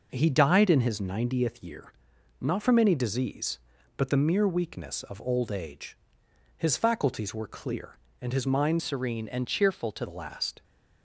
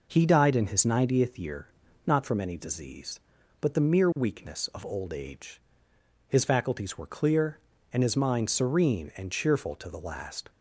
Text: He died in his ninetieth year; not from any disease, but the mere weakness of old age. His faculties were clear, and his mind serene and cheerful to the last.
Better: second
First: changes voice from "serene" to "to"; from 8.7 to 10.0 s; 1.3 s long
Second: none

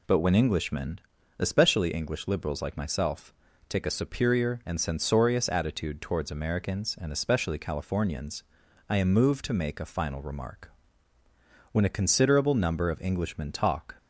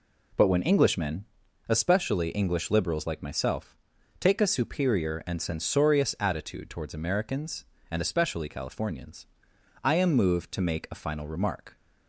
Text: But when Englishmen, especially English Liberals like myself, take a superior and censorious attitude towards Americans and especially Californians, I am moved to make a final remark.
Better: second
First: goes on to say "When a considerable number of Englishmen talk"; strong; from 11.7 s on; 2.2 s long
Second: none

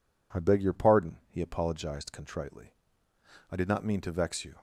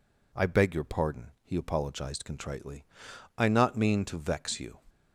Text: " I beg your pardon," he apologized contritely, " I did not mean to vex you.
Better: first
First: none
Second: skips "did"; at 3.4 s

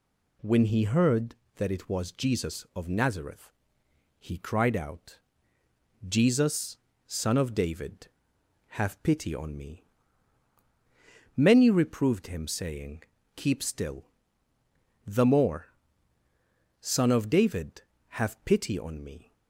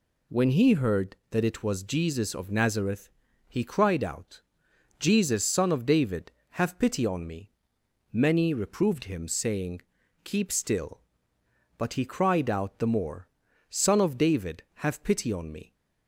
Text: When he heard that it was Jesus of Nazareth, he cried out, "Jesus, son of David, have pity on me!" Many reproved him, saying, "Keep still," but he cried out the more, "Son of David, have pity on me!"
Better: second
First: skips "but he cried out"; at 14.5 s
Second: none

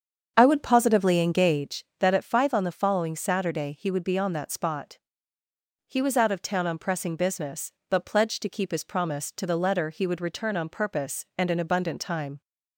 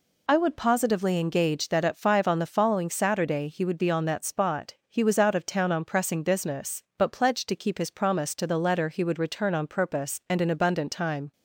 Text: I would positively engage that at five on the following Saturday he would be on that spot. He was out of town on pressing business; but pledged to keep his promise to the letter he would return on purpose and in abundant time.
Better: second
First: starts louder than the rest; strong; until 1.7 s; 7.5 dB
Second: none

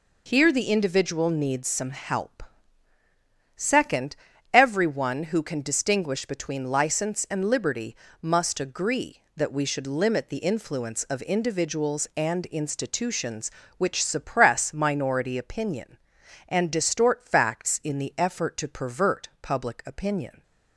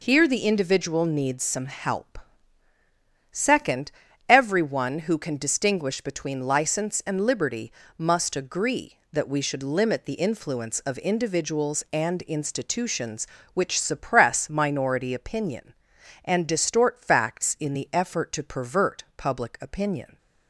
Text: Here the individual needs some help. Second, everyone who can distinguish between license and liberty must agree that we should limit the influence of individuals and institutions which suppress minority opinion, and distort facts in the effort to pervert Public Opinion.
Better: neither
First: pauses between "liberty" and "must"; slight; at 7.9 s; 0.26 s long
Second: pauses between "liberty" and "must"; slight; at 7.7 s; 0.26 s long

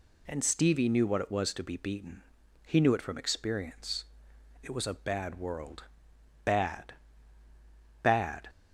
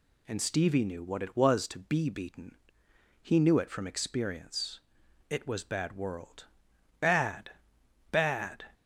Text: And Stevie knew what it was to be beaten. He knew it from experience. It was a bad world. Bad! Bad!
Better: first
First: none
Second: skips "a"; at 5.6 s

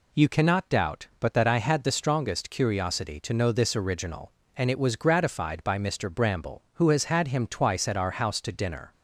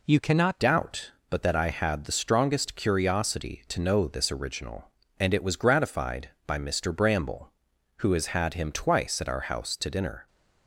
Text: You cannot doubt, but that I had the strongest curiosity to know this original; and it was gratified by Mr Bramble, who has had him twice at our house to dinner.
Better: first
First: none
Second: changes voice at "doubt"; from 0.6 s on; 9.6 s long

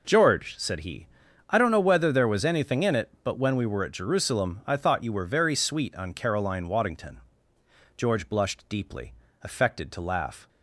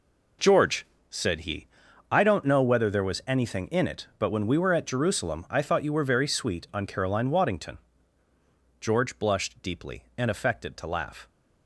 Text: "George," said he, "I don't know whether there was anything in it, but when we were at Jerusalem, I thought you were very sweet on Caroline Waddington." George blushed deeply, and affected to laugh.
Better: second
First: skips "and"; at 9.2 s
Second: none

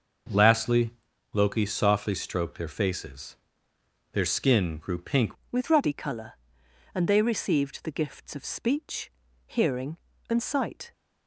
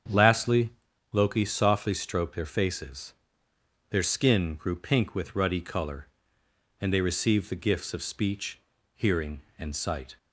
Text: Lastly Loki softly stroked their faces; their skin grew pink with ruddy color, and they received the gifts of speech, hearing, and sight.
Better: second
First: starts louder than the rest; noticeable; until 1.7 s; 6 dB // pauses between "Lastly" and "Loki"; at 0.9 s; 0.40 s long // changes voice at "with"; from 5.4 s on; 5.5 s long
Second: starts louder than the rest; strong; until 1.5 s; 7.5 dB // pauses between "Lastly" and "Loki"; at 0.7 s; 0.40 s long

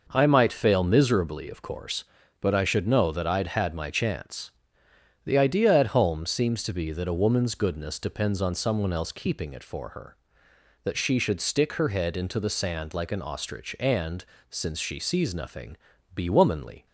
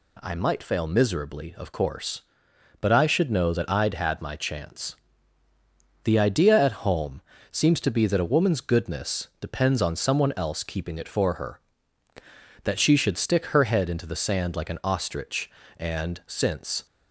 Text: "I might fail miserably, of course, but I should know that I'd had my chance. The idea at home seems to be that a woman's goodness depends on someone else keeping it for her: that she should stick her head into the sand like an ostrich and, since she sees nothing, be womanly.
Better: first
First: none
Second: pauses between "home" and "seems"; slight; at 7.2 s; 0.30 s long // stops before "she sees nothing be womanly"; at 16.8 s

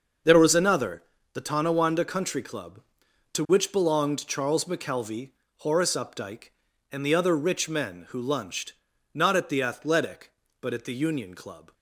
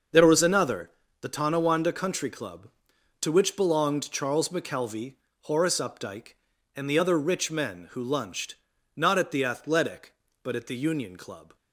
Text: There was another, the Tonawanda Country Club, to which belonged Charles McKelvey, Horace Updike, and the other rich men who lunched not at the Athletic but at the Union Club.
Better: neither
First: starts louder than the rest; noticeable; until 1.5 s; 6 dB // pauses between "lunched" and "not"; at 8.7 s; 0.40 s long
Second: starts louder than the rest; noticeable; until 1.4 s; 6 dB // pauses between "lunched" and "not"; at 8.5 s; 0.40 s long

